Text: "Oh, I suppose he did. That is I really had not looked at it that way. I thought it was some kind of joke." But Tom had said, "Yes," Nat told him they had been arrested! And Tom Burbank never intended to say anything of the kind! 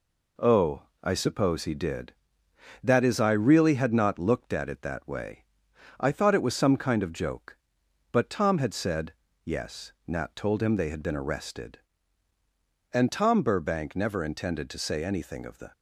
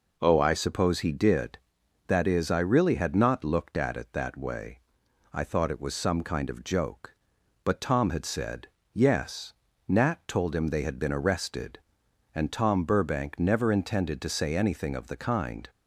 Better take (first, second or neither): second